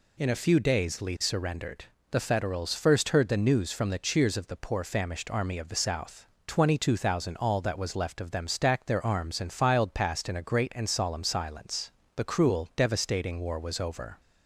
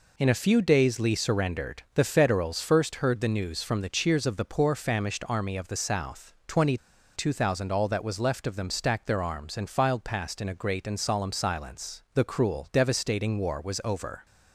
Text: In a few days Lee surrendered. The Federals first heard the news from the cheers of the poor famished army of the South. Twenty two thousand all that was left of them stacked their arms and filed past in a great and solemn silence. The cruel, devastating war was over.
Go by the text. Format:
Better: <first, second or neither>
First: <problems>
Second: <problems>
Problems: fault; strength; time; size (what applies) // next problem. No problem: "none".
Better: first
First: none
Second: pauses between "Twenty" and "two"; at 6.7 s; 0.39 s long